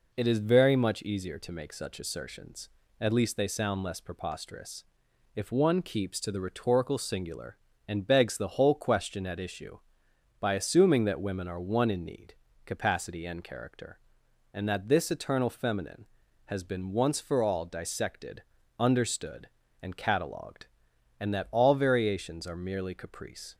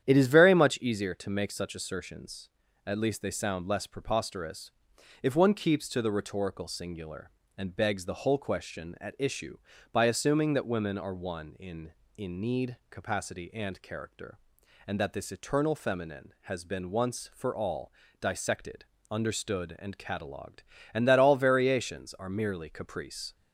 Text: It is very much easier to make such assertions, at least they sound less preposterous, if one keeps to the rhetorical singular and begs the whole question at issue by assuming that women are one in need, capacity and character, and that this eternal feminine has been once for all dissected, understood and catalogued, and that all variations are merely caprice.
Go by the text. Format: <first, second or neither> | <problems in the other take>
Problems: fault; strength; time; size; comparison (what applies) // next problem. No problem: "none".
first | starts louder than the rest; strong; until 1.0 s; 9.5 dB // says "in" twice; at 12.1 s // pauses between "all" and "dissected"; slight; at 17.9 s; 0.26 s long